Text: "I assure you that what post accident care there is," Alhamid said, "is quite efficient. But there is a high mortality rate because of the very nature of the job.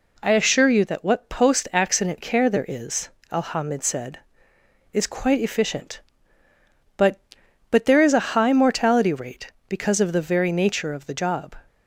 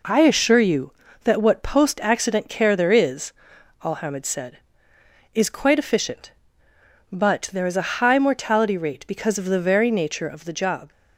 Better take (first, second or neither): second